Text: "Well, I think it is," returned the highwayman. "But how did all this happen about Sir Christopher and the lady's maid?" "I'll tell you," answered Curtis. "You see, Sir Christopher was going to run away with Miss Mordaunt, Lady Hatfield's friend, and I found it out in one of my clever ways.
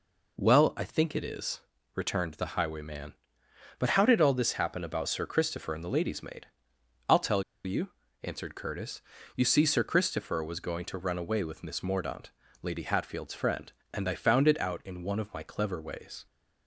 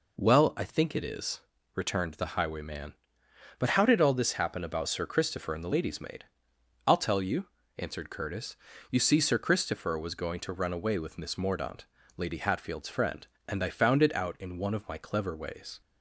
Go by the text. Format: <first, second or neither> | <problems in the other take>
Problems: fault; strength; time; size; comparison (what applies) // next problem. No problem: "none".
second | pauses between "tell" and "you"; slight; at 7.4 s; 0.22 s long